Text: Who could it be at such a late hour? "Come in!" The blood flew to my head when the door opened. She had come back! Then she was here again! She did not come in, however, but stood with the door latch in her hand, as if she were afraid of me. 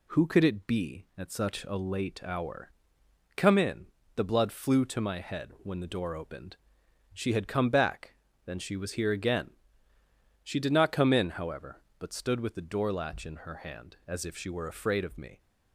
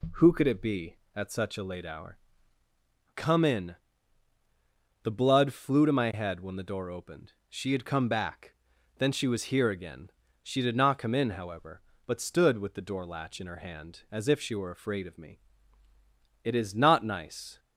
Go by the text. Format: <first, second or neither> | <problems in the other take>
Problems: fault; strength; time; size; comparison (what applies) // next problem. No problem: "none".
first | goes on to say "It is not nice"; noticeable; from 16.4 s on; 1.1 s long